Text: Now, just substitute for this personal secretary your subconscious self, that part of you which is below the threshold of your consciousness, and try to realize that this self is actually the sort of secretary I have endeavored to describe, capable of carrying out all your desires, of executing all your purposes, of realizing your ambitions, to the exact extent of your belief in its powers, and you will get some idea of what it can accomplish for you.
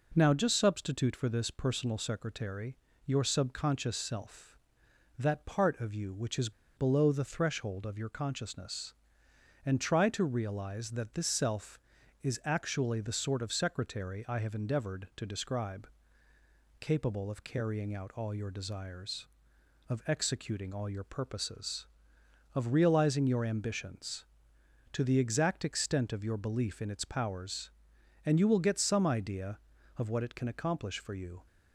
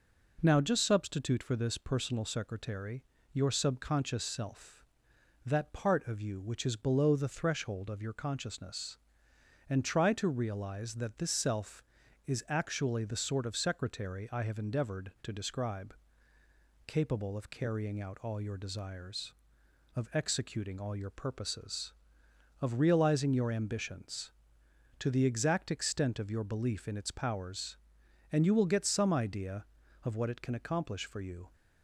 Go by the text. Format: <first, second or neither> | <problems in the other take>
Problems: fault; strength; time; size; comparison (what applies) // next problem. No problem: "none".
second | pauses between "secretary" and "your"; slight; at 2.7 s; 0.30 s long; slight in the second // pauses between "is" and "below"; slight; at 6.5 s; 0.25 s long